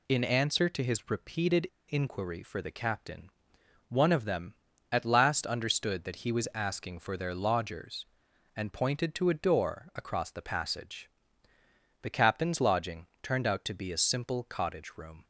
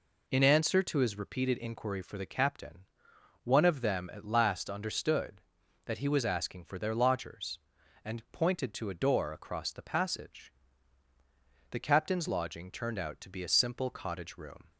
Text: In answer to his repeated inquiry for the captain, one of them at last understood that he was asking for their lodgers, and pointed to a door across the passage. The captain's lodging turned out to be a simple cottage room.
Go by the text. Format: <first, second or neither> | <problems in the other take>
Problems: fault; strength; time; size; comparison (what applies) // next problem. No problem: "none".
second | pauses between "repeated" and "inquiry"; slight; at 1.6 s; 0.24 s long